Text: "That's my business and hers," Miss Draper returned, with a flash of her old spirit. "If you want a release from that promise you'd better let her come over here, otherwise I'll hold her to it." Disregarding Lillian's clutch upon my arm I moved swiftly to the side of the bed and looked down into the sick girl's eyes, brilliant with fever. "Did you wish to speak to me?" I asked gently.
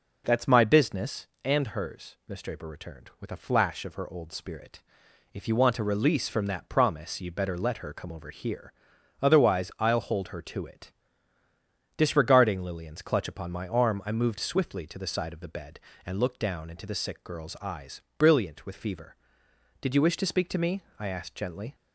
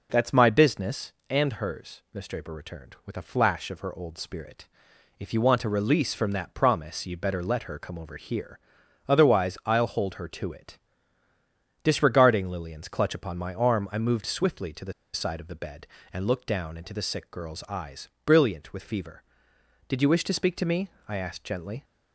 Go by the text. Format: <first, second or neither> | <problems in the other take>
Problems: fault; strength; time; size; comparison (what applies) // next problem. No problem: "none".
first | pauses between "the" and "side"; slight; at 14.9 s; 0.20 s long